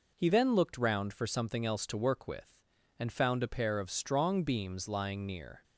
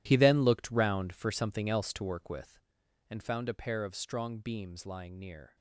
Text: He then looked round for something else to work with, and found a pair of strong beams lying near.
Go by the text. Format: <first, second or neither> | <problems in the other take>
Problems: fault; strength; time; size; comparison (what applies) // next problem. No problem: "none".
first | gets quieter; strong; throughout; 14 dB